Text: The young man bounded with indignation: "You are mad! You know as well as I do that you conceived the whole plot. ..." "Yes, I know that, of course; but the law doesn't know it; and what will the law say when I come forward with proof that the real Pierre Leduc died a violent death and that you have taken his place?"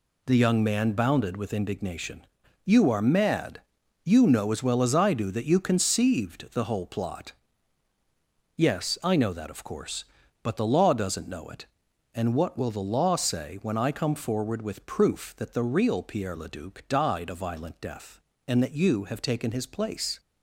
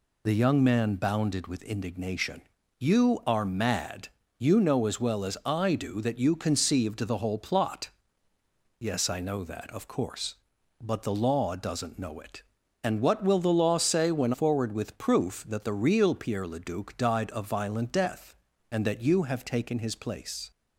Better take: first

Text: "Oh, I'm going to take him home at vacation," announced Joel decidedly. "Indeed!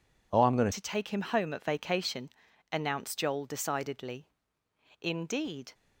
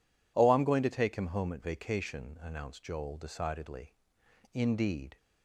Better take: second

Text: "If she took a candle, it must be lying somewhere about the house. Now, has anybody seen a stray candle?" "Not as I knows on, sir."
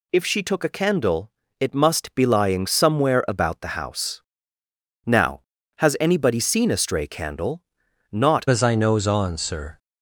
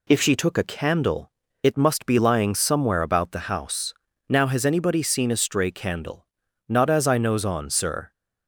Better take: second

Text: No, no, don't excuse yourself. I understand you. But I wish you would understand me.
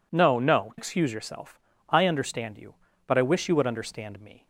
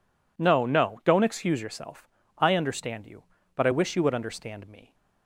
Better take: second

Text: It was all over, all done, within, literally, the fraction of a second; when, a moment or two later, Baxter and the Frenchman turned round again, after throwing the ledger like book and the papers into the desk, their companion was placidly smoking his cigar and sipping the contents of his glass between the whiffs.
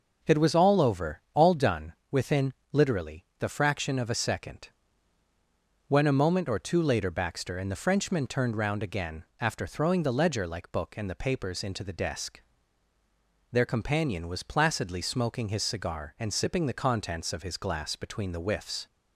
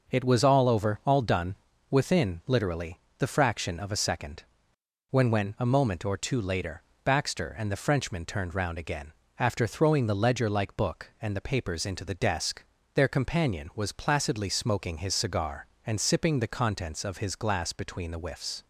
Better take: first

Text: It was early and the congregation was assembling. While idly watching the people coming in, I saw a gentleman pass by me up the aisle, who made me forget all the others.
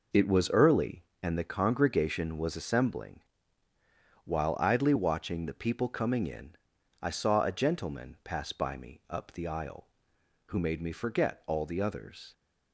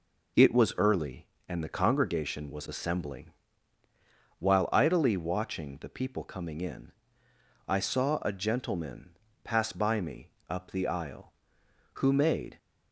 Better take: first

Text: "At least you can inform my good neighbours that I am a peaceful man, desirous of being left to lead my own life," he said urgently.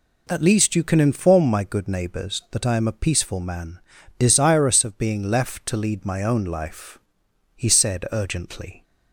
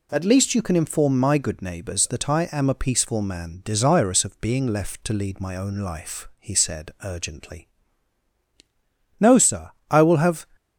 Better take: first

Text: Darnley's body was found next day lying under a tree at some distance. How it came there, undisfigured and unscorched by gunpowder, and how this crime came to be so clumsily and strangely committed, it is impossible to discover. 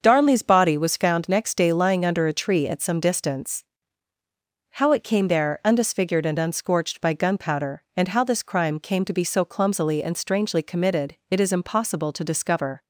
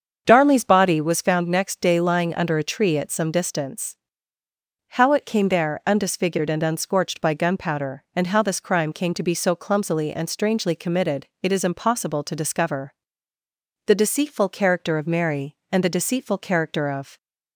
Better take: first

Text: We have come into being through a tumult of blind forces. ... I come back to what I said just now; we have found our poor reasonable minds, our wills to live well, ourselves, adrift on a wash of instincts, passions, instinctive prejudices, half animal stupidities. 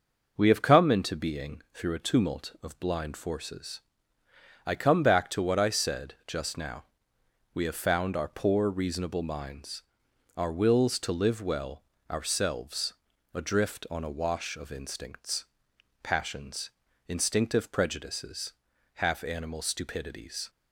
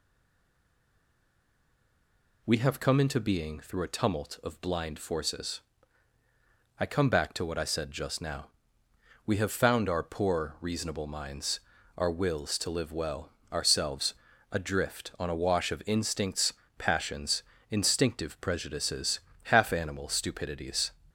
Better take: first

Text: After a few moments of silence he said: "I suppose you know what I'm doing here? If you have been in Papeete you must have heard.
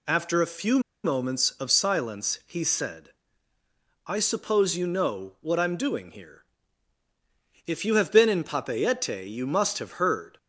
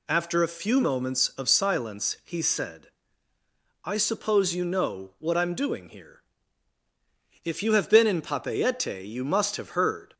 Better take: second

